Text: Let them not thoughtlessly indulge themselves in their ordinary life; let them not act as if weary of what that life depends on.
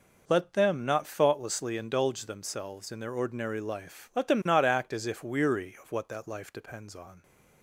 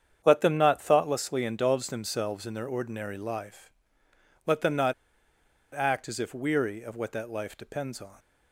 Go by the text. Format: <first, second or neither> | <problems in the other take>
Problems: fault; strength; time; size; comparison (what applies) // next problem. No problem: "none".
first | starts louder than the rest; strong; until 1.2 s; 8 dB // pauses between "not" and "act"; noticeable; at 4.9 s; 0.81 s long